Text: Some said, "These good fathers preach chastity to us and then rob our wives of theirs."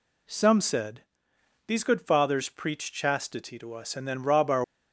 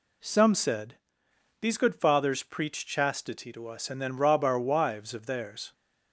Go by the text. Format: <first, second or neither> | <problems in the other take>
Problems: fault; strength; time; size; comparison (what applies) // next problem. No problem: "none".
second | stops before "wives of theirs"; at 4.6 s